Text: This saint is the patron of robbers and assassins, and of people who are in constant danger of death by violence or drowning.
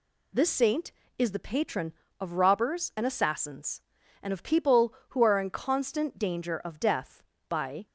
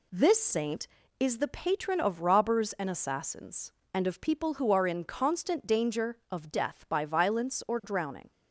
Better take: second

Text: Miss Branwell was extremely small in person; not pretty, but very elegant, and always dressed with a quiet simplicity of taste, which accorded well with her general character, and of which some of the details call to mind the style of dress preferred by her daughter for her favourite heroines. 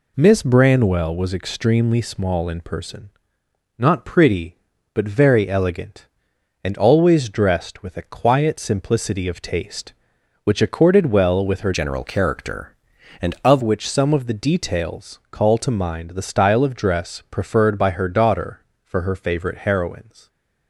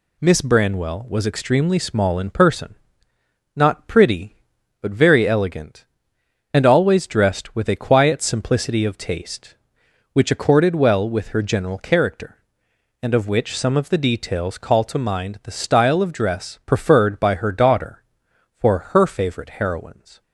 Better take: second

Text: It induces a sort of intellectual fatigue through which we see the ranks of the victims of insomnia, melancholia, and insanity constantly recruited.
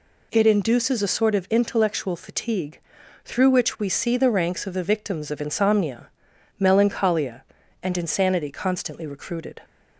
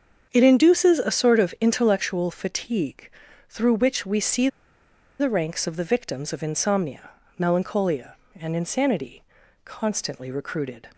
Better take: first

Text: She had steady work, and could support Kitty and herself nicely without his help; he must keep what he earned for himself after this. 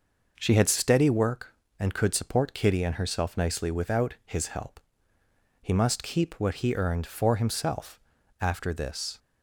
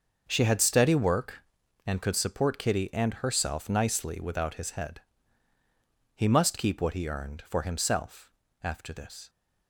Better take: first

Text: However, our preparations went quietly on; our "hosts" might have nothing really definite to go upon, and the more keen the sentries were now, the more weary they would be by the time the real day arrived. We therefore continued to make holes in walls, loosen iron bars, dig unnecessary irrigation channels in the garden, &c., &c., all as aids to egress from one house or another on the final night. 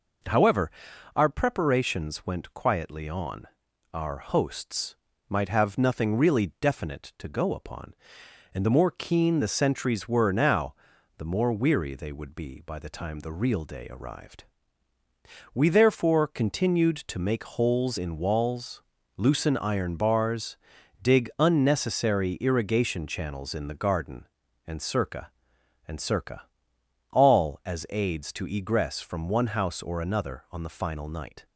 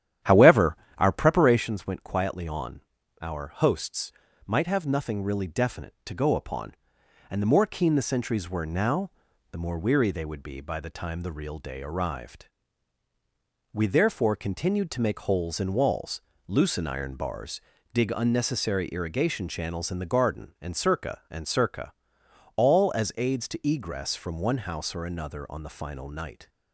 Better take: first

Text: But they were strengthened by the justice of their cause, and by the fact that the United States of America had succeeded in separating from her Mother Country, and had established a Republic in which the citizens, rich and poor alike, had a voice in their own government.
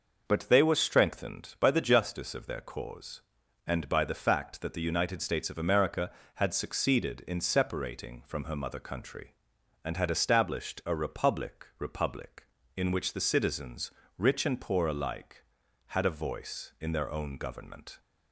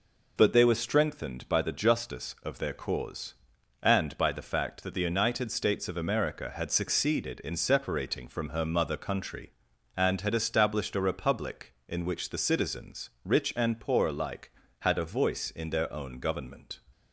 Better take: second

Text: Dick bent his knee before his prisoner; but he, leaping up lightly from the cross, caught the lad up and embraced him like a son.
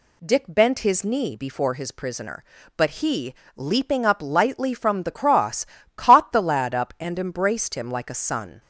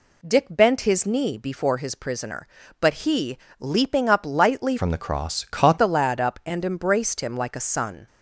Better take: first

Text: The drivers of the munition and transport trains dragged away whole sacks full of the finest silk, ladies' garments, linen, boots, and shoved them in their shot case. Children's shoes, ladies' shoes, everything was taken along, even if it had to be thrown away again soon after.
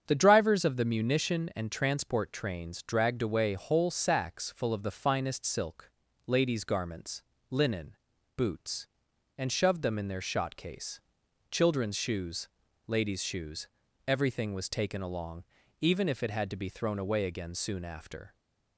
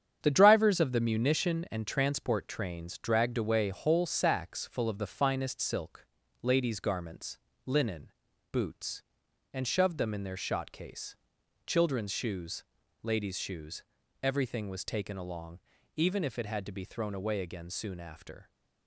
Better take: first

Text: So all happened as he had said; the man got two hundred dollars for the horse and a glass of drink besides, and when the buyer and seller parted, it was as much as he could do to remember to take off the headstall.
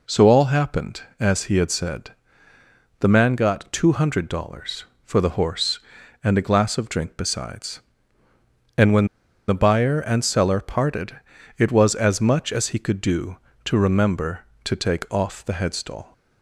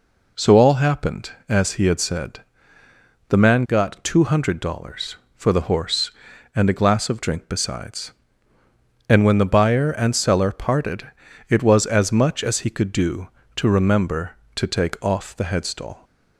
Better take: second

